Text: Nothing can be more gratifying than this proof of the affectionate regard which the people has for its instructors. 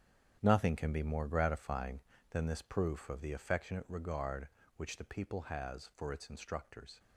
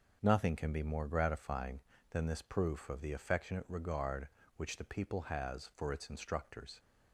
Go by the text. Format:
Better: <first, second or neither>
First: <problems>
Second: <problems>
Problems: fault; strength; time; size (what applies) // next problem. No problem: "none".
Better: second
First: gets quieter; strong; throughout; 11 dB // starts louder than the rest; strong; until 1.4 s; 9 dB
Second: starts louder than the rest; noticeable; until 1.2 s; 6 dB